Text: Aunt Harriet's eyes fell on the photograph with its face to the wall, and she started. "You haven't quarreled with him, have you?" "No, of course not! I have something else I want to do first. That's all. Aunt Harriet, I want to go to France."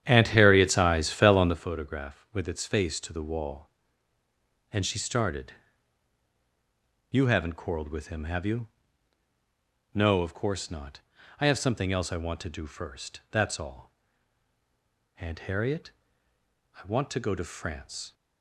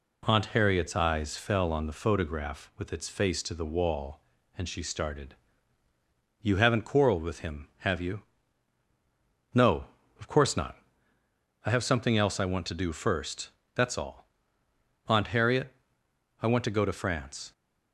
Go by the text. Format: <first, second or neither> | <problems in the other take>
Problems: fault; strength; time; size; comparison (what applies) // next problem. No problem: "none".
second | starts louder than the rest; strong; until 1.7 s; 10 dB